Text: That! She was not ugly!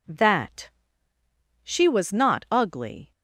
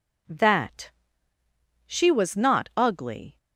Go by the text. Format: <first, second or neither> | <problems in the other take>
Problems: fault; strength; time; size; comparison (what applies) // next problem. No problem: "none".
neither | none